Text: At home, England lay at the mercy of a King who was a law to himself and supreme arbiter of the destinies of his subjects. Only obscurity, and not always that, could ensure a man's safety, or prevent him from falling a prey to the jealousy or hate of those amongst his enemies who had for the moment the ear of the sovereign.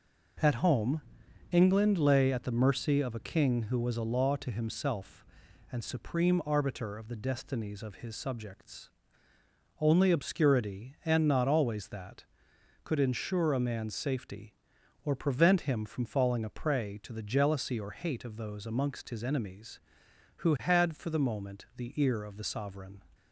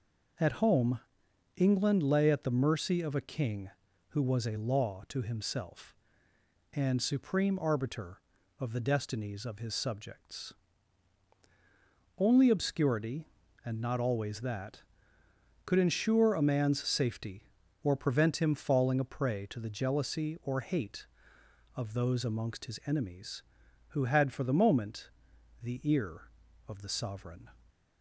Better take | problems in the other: first | skips "from"; at 18.5 s // pauses between "moment" and "the"; noticeable; at 25.0 s; 0.52 s long

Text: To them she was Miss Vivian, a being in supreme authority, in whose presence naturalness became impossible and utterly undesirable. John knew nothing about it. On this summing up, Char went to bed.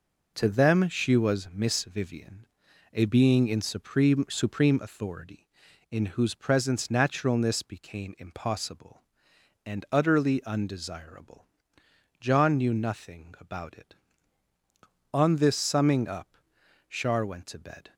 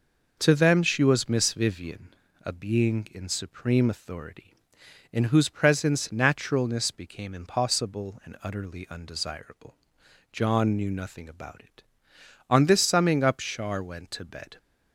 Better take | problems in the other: second | says "supreme" twice; at 4.2 s

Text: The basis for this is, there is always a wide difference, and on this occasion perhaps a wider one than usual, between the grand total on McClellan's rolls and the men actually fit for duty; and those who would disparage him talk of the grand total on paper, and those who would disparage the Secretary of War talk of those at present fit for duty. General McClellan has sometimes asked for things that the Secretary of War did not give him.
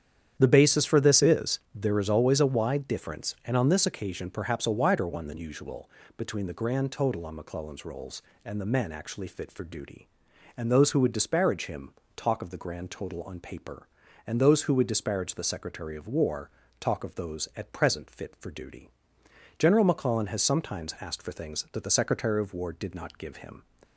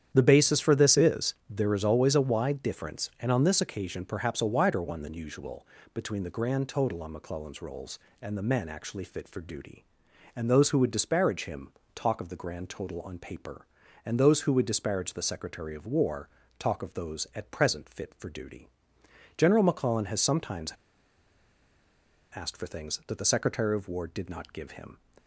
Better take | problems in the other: first | starts louder than the rest; strong; until 1.1 s; 9.5 dB; strong in the first // pauses between "him" and "talk"; slight; at 11.7 s; 0.22 s long; slight in the first // pauses between "War" and "talk"; slight; at 16.2 s; 0.30 s long; slight in the first // pauses between "sometimes" and "asked"; strong; at 20.7 s; 1.6 s long

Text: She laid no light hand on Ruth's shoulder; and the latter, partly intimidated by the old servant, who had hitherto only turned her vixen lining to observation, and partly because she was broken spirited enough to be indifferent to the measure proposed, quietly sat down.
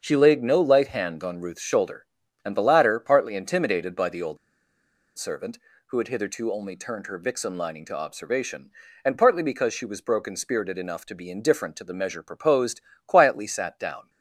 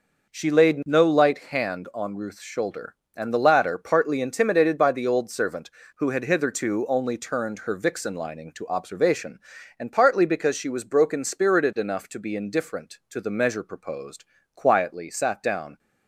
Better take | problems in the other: second | starts louder than the rest; until 1.0 s; 7 dB // pauses between "old" and "servant"; noticeable; at 4.3 s; 0.80 s long

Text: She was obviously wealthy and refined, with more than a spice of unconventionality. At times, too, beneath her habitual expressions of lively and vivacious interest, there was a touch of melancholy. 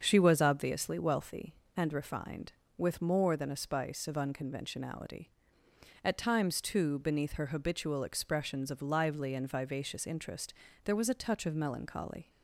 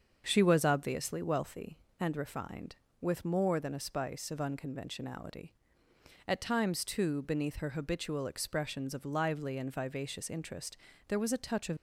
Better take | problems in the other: first | starts louder than the rest; until 1.2 s; 6.5 dB; also in the first // stops before "melancholy"; at 11.7 s

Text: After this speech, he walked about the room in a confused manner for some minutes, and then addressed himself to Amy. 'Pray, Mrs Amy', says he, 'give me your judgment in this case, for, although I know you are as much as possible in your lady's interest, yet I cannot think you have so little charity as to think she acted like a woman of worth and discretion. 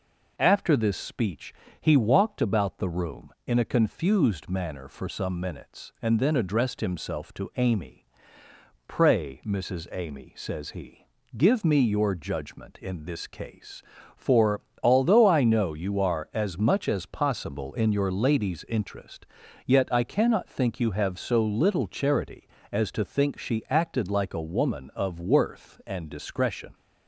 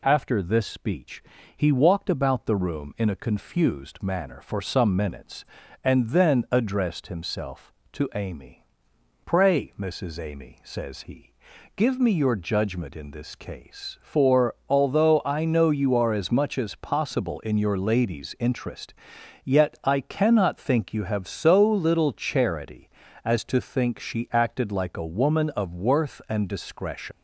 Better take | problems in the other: first | leaves "discretion" unfinished; at 27.1 s; 125 ms

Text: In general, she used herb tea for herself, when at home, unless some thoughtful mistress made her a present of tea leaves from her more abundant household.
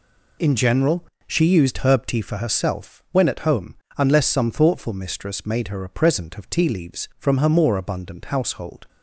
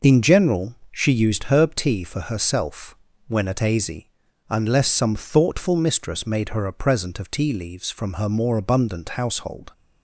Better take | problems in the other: first | says "azy" for "home"; at 3.5 s

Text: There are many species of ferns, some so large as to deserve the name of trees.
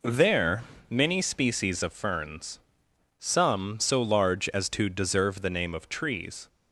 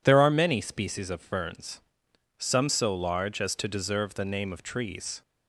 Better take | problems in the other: second | skips "are"; at 0.7 s

